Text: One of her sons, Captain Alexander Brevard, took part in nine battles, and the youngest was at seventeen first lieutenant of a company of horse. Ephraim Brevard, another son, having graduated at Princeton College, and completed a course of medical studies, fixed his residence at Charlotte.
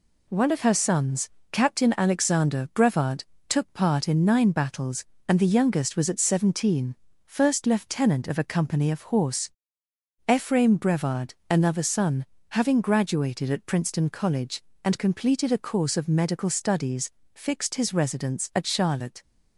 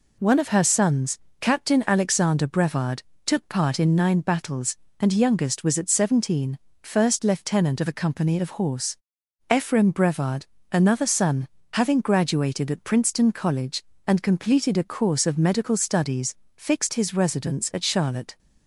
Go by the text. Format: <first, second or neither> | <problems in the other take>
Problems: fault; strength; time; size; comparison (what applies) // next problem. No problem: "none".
first | skips "the"; at 5.1 s // pauses between "seventeen" and "first"; slight; at 6.5 s; 0.24 s long; slight in the first